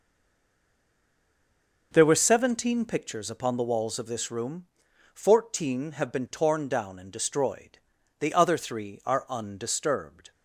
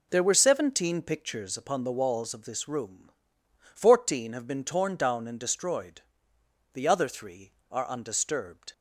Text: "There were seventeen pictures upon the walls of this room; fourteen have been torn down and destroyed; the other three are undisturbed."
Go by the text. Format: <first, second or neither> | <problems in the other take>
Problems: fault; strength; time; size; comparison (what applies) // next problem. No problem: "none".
second | stays silent before the first word; noticeable; until 1.9 s; 1.9 s long